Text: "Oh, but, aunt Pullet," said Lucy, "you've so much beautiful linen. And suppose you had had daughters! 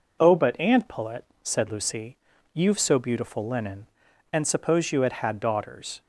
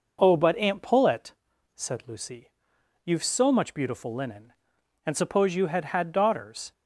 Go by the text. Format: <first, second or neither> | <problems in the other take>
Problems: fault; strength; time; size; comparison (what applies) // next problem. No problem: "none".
second | skips "much"; at 2.9 s